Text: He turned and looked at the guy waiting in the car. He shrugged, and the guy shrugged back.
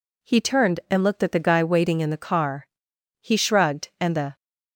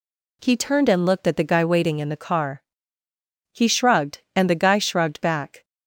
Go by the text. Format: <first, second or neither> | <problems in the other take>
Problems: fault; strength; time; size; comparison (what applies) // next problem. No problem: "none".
second | stops before "guy shrugged back"; at 4.3 s